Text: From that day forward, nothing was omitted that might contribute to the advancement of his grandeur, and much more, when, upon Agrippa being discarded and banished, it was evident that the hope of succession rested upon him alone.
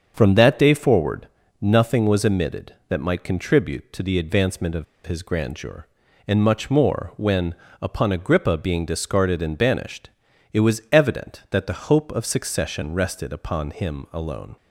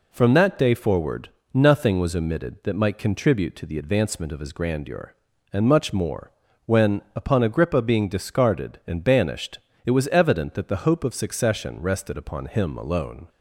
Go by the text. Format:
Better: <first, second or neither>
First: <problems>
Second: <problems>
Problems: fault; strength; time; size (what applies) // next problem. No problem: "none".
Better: second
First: starts louder than the rest; until 1.1 s; 7 dB // pauses between "of" and "his"; slight; at 4.8 s; 0.21 s long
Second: none